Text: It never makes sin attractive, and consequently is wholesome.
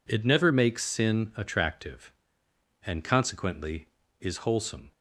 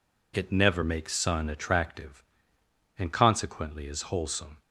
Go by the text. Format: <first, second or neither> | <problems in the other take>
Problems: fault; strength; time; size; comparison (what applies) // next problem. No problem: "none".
first | says "sun" for "sin"; at 1.1 s